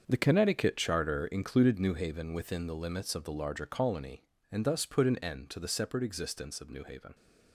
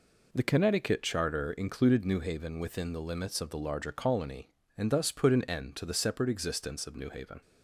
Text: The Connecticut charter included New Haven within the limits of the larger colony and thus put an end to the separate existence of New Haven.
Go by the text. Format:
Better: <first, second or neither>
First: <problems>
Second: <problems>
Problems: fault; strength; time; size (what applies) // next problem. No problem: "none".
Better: second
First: gets quieter; strong; throughout; 11 dB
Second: none